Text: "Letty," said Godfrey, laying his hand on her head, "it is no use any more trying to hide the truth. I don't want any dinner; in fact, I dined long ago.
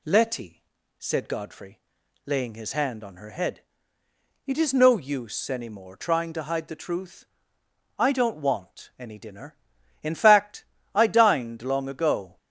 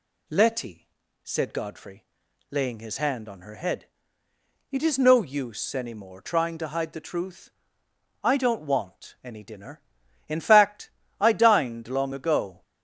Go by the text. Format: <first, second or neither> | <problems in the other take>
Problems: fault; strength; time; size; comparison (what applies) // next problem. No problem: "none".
neither | none